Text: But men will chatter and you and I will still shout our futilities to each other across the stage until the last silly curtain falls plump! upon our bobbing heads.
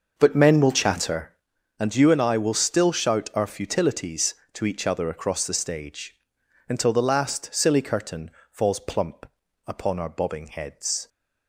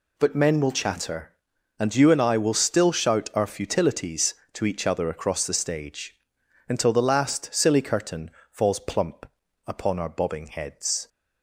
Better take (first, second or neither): second